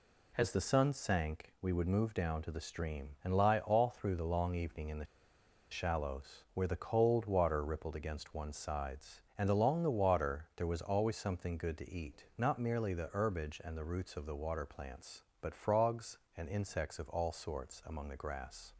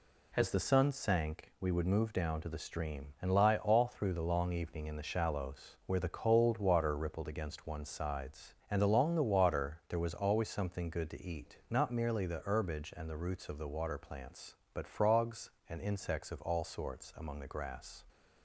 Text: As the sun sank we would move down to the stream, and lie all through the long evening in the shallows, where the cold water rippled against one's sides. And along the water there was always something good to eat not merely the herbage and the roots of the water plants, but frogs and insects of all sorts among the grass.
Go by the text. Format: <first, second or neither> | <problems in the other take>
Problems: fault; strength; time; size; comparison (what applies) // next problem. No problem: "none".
second | pauses between "the" and "shallows"; noticeable; at 5.0 s; 0.65 s long